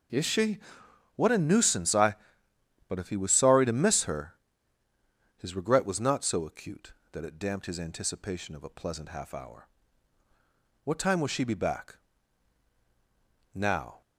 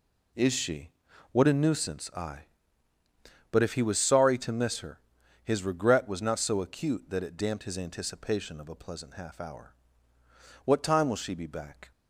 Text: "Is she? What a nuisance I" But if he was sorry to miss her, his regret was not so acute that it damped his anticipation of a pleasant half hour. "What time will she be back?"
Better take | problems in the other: second | goes on to say "Now"; slight; from 13.5 s on; 0.46 s long

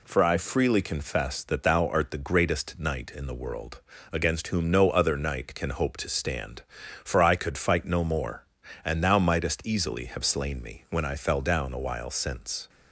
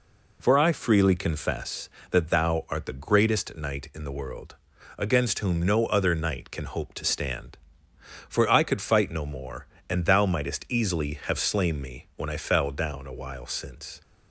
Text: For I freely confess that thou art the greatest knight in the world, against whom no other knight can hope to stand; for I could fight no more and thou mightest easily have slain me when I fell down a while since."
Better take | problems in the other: neither | none

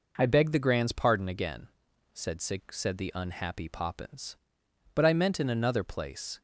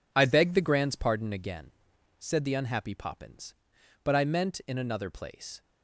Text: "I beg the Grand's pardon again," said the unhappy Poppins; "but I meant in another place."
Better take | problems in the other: second | says "said" twice; at 2.4 s

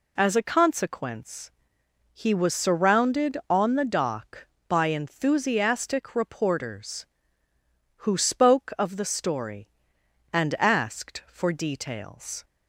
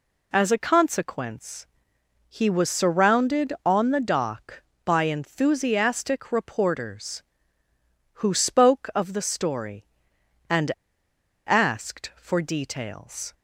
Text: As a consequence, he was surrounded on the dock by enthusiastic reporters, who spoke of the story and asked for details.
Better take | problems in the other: first | pauses between "and" and "asked"; noticeable; at 10.7 s; 0.76 s long

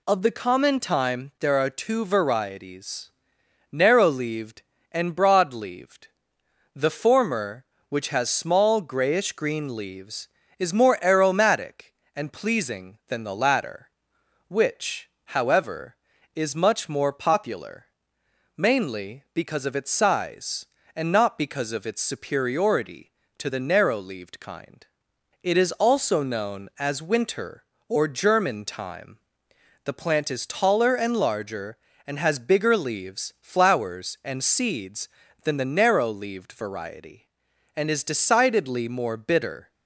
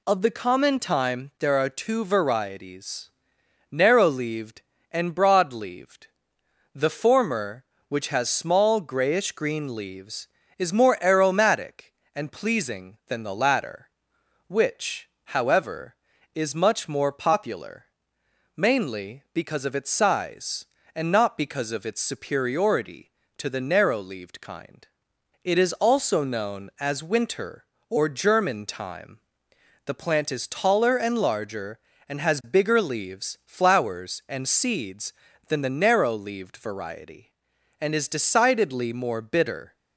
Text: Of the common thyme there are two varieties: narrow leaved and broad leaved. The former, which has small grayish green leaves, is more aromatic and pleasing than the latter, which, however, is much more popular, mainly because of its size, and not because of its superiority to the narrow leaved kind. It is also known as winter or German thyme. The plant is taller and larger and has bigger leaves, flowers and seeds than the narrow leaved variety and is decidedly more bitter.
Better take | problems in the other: neither | none

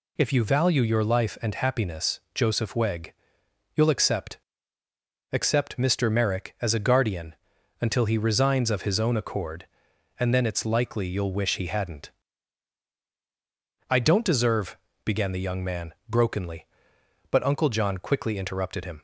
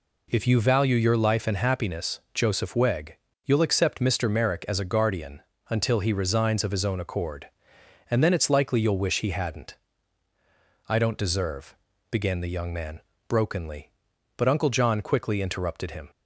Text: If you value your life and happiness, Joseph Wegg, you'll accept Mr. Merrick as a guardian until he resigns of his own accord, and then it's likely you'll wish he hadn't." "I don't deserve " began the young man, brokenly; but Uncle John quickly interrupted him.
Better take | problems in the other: second | says "accept" twice; at 5.3 s // pauses between "guardian" and "until"; noticeable; at 7.3 s; 0.46 s long; slight in the second

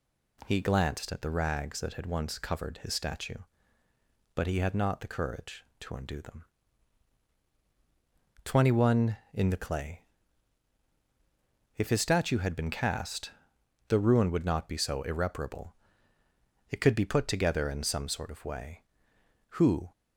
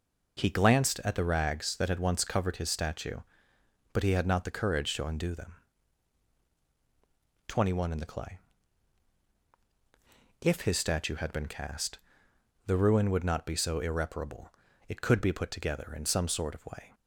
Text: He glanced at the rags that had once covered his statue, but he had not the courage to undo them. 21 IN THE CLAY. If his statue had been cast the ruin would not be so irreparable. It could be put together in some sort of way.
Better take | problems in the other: second | pauses between "cast" and "the"; noticeable; at 13.3 s; 0.58 s long; noticeable in the second // goes on to say "Who"; slight; from 19.5 s on; 0.40 s long

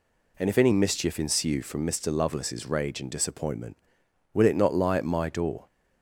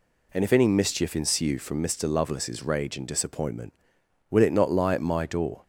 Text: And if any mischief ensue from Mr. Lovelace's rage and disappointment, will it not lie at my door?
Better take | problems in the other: neither | none

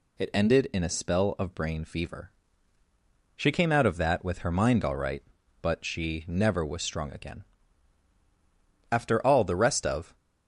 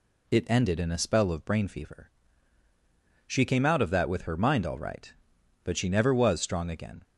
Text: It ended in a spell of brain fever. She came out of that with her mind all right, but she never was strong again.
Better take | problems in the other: second | goes on to say "After all the rest of"; noticeable; from 8.9 s on; 1.2 s long

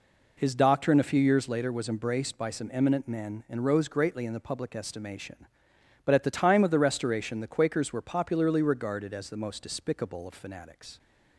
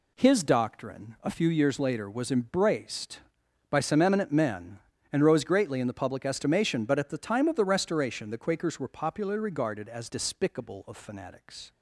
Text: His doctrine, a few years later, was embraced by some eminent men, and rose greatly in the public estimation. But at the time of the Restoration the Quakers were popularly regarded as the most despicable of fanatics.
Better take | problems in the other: first | skips "the most"; at 10.0 s

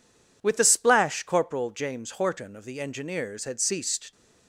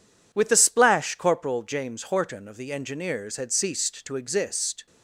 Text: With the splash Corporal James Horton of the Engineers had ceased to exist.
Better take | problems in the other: second | stops before "to exist"; at 4.1 s

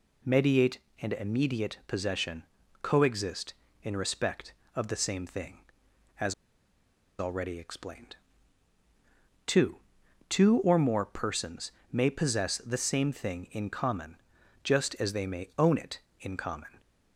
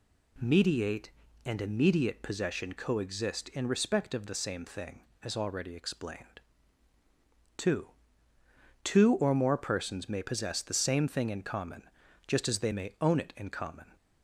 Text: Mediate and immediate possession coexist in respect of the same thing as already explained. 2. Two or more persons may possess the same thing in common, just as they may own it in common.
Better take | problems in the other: second | pauses between "possession" and "coexist"; at 2.4 s; 0.38 s long // pauses between "as" and "already"; noticeable; at 6.3 s; 0.86 s long // pauses between "persons" and "may"; slight; at 11.7 s; 0.22 s long

